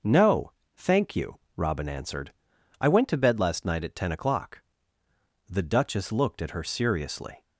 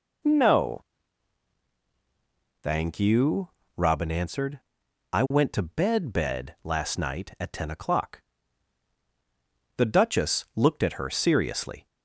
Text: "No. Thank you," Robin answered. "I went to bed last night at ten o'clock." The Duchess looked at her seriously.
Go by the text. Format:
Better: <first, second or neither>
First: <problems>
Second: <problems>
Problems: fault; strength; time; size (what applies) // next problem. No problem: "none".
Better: first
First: none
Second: says "bed" twice; at 6.1 s